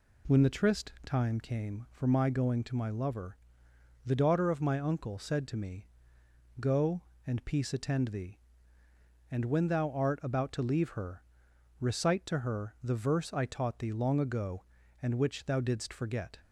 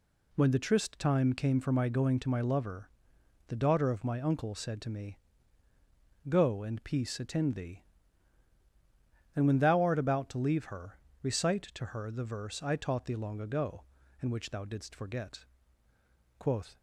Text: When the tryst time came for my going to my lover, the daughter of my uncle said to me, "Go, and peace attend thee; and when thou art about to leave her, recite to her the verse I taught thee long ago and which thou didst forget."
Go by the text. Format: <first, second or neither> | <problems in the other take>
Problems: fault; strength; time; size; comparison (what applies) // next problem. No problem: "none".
first | goes on to say "Quoth"; slight; from 16.3 s on; 0.38 s long